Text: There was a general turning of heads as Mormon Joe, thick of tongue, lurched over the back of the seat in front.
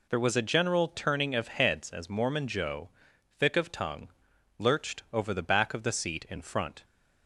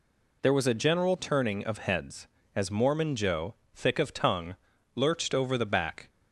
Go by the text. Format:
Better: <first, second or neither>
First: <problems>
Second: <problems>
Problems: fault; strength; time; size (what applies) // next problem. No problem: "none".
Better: first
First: none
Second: stops before "of the seat in front"; at 6.0 s